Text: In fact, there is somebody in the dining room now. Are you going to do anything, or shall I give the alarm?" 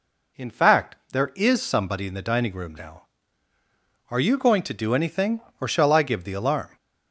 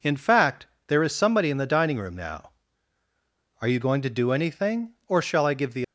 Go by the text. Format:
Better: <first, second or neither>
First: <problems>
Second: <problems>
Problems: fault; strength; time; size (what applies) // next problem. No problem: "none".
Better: first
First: none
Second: stops before "alarm"; at 5.8 s